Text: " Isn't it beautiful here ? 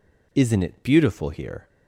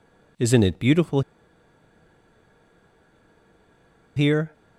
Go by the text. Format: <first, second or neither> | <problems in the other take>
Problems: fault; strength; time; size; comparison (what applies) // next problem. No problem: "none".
first | pauses between "beautiful" and "here"; strong; at 1.2 s; 2.9 s long